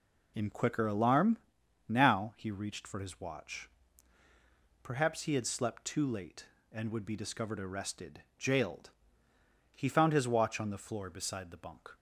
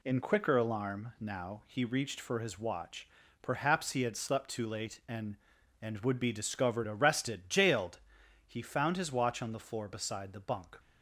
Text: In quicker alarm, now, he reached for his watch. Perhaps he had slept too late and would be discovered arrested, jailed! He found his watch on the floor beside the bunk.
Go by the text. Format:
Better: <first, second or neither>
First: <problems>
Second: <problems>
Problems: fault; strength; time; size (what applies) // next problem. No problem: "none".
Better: first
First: none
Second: says "and" twice; at 5.8 s